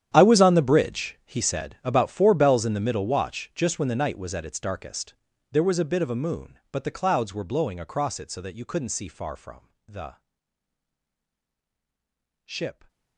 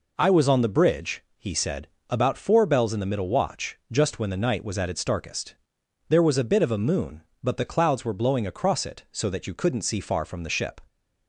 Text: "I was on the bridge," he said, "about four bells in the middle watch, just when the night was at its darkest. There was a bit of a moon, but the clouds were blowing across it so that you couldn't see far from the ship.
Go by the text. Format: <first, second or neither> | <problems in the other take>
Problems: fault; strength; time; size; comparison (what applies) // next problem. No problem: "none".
second | gets quieter; strong; throughout; 20 dB // pauses between "from" and "the"; slight; at 9.6 s; 0.18 s long // pauses between "the" and "ship"; strong; at 10.1 s; 2.2 s long